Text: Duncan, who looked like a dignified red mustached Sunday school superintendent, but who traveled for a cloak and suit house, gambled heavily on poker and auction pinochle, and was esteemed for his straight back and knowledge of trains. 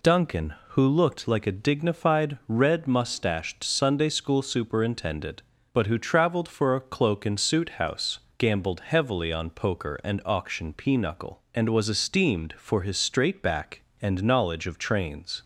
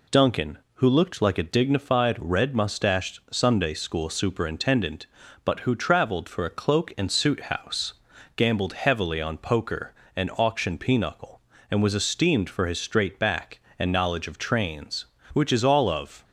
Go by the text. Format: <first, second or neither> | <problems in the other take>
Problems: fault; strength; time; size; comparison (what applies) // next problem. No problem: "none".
first | goes on to say "Which is all of"; noticeable; from 15.3 s on; 0.88 s long